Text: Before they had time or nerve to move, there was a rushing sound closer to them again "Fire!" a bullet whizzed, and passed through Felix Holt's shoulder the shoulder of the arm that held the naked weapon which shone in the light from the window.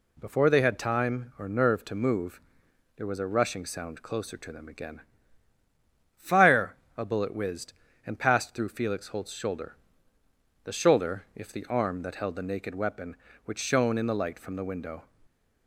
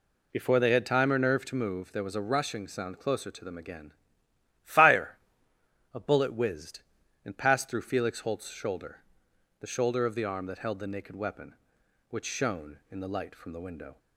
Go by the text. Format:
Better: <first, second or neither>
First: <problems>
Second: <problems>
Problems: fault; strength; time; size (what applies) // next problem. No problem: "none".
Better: second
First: pauses between "again" and "Fire"; at 5.0 s; 1.1 s long // pauses between "shoulder" and "the"; noticeable; at 9.7 s; 0.88 s long // says "if" for "of"; at 11.3 s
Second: pauses between "again" and "Fire"; noticeable; at 3.9 s; 0.72 s long // pauses between "shoulder" and "the"; noticeable; at 9.0 s; 0.56 s long